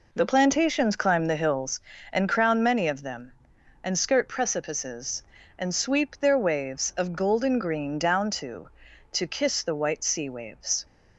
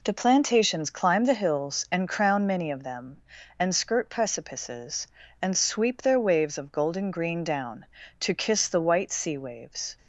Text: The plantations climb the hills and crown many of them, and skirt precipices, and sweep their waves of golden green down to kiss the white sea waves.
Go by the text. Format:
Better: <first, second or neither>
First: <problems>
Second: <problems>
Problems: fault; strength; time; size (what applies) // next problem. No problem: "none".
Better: second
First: says "to" twice; at 9.1 s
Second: none